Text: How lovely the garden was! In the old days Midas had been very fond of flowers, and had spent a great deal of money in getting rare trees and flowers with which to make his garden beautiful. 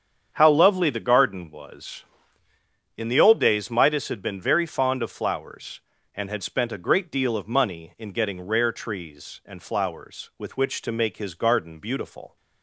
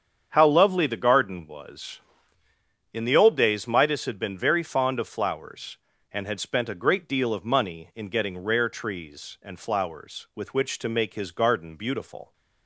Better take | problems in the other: neither | starts louder than the rest; strong; the same in both

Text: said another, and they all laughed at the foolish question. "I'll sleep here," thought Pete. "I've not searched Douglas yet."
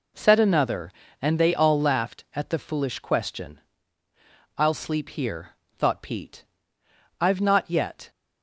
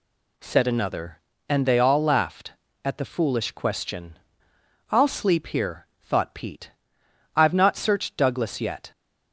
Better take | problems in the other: second | skips "searched Douglas"; at 7.6 s

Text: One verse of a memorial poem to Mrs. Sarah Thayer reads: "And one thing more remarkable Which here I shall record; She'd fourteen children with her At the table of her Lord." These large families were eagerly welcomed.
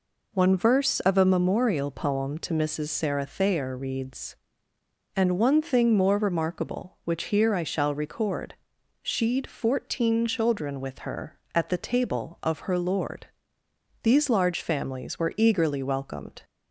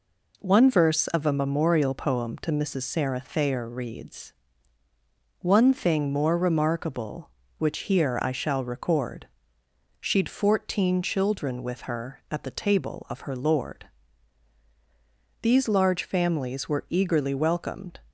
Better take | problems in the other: first | skips "And"; at 4.8 s

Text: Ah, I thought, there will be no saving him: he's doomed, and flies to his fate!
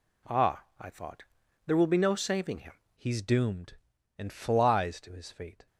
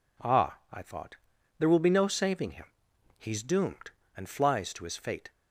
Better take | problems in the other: second | changes voice at "he's"; from 2.9 s on; 2.7 s long

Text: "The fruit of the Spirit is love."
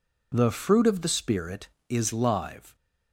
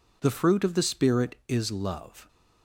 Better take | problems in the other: second | says "live" for "love"; at 2.1 s

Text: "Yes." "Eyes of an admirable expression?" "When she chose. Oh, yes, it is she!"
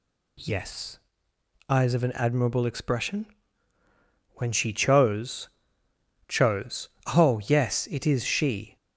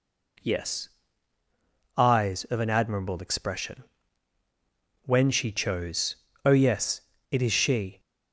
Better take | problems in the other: second | says "chose" twice; at 6.2 s

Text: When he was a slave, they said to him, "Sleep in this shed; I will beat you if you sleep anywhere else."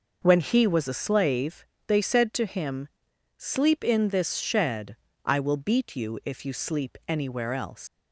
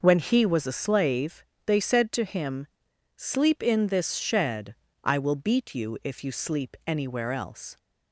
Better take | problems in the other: second | leaves "else" unfinished; at 7.8 s; 115 ms

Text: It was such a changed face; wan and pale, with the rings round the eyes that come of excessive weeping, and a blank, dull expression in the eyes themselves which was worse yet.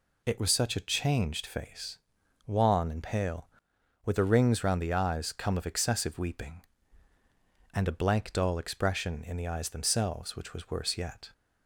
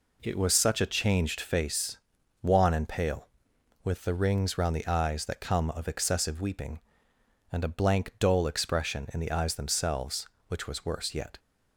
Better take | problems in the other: second | skips "that"; at 5.3 s

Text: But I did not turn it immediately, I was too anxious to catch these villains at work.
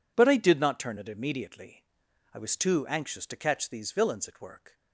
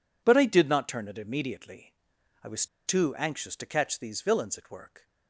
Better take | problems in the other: first | pauses between "was" and "too"; slight; at 2.6 s; 0.21 s long

